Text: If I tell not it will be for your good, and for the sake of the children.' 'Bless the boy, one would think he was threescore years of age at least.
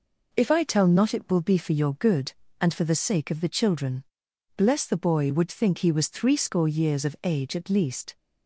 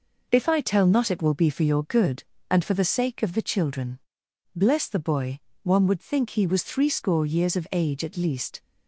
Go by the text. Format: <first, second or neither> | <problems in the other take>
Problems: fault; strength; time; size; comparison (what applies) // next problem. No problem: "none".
second | skips "one"; at 5.3 s